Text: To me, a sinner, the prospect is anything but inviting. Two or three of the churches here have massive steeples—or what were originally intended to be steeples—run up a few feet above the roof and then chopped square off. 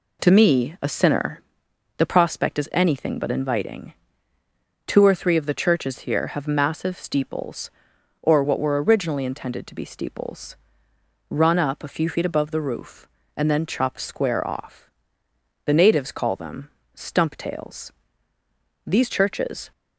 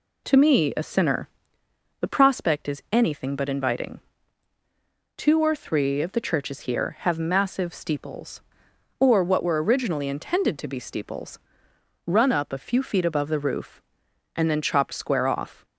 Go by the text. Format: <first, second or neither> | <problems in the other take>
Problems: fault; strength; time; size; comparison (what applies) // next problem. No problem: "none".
second | goes on to say "The natives call them stump tails These churches"; strong; from 15.6 s on; 4.0 s long